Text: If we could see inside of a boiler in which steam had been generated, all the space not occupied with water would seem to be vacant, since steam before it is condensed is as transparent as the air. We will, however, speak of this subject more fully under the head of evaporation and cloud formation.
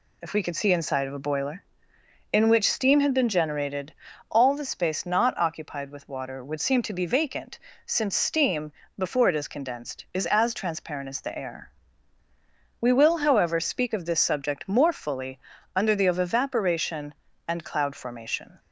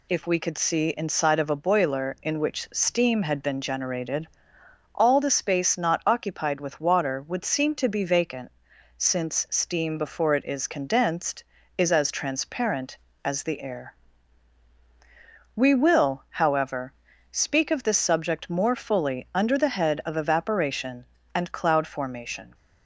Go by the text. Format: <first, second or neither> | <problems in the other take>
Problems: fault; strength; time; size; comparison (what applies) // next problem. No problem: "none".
second | pauses between "steam" and "before"; slight; at 8.7 s; 0.28 s long // pauses between "fully" and "under"; slight; at 15.3 s; 0.36 s long // skips "head"; at 16.0 s